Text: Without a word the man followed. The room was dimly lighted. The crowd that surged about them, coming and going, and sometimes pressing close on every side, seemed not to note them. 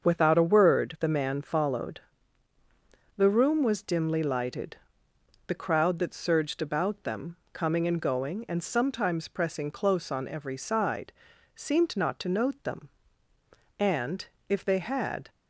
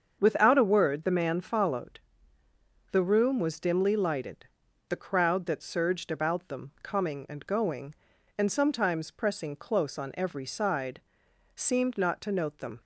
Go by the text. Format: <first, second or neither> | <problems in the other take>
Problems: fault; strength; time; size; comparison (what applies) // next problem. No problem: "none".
second | starts louder than the rest; until 1.0 s; 6.5 dB; also in the second // goes on to say "And if they had"; from 13.8 s on; 1.4 s long